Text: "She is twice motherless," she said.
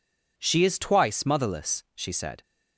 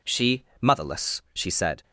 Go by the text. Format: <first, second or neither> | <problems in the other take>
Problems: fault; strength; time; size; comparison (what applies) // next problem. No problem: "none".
first | skips "is twice"; at 0.5 s